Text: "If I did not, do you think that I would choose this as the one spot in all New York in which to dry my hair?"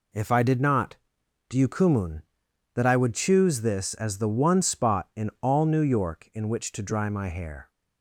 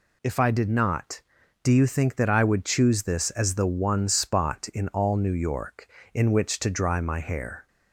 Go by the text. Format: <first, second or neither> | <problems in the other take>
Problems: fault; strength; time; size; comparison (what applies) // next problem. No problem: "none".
second | says "kumun" for "think"; at 1.6 s